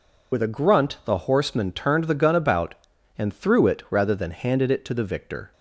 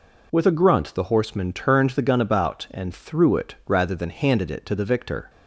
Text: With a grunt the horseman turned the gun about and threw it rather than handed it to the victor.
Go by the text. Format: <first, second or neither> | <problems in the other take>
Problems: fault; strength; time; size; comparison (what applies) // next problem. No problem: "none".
second | loses the start of "With"; at 0.3 s; 55 ms